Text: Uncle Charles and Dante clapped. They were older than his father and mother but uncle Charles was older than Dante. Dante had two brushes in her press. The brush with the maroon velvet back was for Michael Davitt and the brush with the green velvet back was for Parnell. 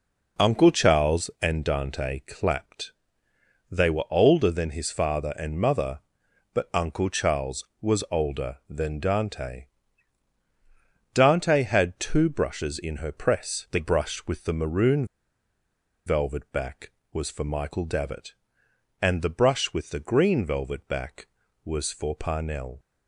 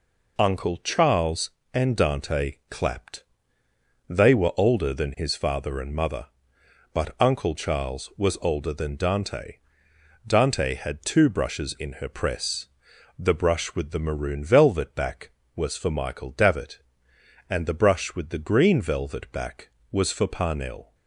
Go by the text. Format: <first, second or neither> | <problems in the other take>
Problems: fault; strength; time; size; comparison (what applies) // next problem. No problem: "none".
second | pauses between "maroon" and "velvet"; at 15.0 s; 1.0 s long